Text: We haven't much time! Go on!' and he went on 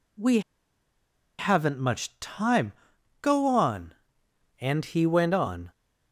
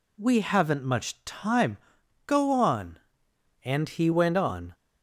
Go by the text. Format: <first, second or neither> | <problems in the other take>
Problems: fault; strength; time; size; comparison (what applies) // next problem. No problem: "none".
second | pauses between "We" and "haven't"; at 0.3 s; 0.98 s long